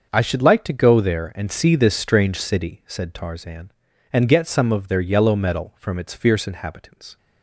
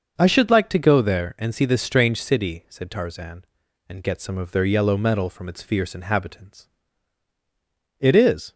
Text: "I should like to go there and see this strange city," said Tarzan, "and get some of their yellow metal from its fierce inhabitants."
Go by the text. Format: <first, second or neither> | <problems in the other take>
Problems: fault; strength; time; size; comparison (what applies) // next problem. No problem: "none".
first | starts louder than the rest; until 1.2 s; 6.5 dB; also in the first // goes on to say "It is"; from 7.9 s on; 0.54 s long